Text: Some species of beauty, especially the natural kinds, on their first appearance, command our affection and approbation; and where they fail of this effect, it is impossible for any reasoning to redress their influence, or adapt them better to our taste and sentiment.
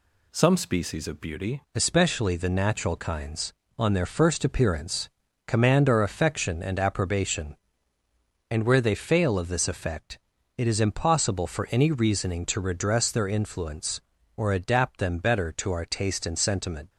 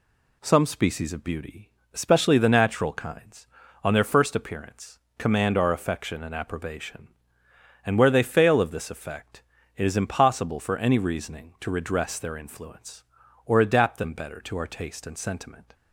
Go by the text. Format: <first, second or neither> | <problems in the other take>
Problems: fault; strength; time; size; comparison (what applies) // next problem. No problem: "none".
second | changes voice at "especially"; from 1.7 s on; 15.1 s long